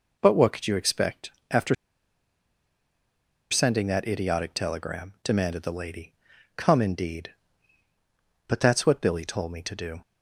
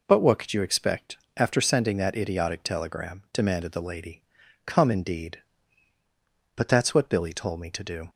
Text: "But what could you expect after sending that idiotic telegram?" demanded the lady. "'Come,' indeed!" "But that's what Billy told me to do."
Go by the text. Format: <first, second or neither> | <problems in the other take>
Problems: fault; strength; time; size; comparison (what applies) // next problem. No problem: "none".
second | pauses between "expect" and "after"; slight; at 1.2 s; 0.22 s long; slight in the second // pauses between "after" and "sending"; strong; at 1.7 s; 1.7 s long